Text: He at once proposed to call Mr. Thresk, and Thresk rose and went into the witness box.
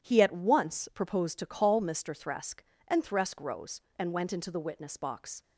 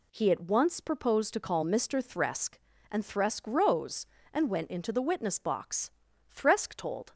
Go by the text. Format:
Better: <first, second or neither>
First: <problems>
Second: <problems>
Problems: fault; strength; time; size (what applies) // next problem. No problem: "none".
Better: first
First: none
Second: goes on to say "Thresk told"; noticeable; from 6.3 s on; 0.80 s long